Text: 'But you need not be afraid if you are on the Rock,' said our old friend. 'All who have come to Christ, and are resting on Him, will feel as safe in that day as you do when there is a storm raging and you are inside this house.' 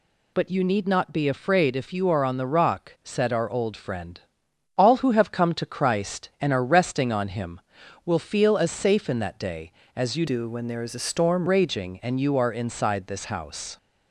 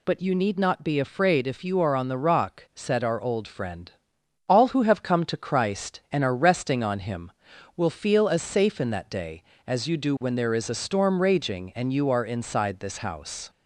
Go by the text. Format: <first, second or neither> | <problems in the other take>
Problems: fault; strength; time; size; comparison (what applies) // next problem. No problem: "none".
second | changes voice from "do" to "storm"; from 10.2 to 11.4 s; 1.2 s long